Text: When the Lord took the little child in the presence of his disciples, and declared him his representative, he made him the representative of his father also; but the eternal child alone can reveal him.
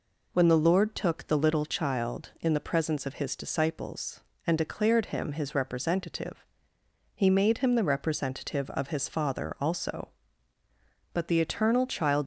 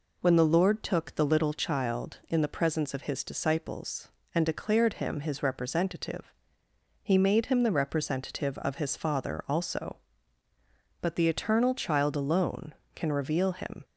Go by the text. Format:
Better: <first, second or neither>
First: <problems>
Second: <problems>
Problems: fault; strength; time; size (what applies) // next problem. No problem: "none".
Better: second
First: stops before "alone can reveal him"; at 12.2 s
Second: none